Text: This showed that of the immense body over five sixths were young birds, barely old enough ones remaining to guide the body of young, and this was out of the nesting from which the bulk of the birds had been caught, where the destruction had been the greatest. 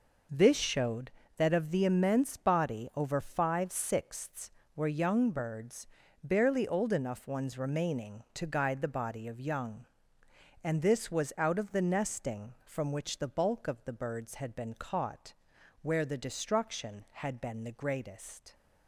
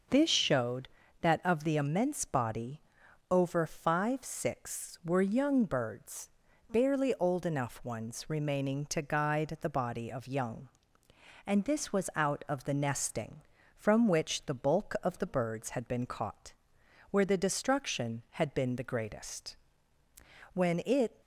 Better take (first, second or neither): first